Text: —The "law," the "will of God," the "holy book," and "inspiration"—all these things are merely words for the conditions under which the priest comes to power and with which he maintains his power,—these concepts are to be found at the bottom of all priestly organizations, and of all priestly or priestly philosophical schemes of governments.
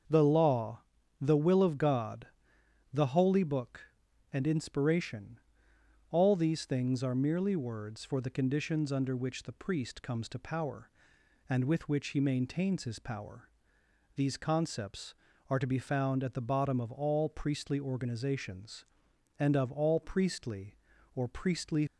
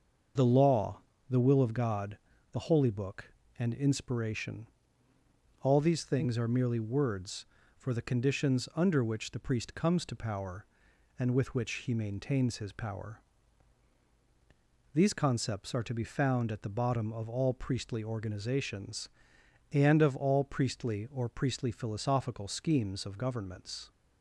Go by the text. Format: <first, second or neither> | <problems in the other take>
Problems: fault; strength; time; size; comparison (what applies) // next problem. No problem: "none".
second | starts louder than the rest; until 1.4 s; 6.5 dB; also in the second // stops before "philosophical schemes of governments"; at 21.8 s